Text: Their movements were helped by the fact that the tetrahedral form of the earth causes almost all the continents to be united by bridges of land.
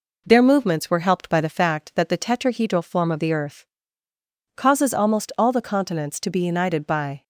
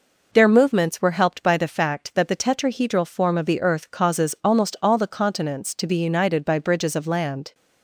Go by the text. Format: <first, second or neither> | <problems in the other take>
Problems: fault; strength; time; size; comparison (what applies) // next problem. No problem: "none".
second | pauses between "earth" and "causes"; noticeable; at 3.6 s; 0.92 s long // stops before "bridges of land"; at 7.2 s